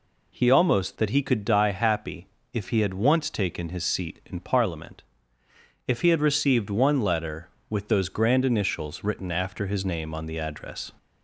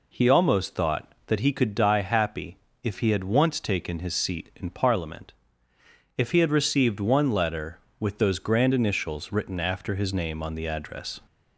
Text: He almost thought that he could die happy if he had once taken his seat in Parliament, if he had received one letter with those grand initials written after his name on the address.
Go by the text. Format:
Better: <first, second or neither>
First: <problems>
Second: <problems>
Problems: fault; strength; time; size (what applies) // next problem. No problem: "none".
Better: second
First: skips "thought"; at 0.9 s // pauses between "happy" and "if"; slight; at 2.2 s; 0.26 s long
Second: pauses between "happy" and "if"; slight; at 2.5 s; 0.26 s long